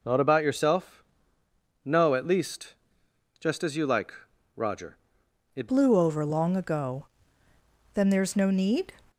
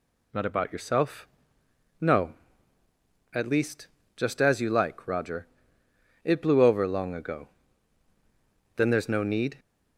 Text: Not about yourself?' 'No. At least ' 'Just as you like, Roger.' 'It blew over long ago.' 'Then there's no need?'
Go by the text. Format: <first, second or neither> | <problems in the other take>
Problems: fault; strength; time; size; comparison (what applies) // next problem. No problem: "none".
second | changes voice at "blew"; from 5.6 s on; 3.3 s long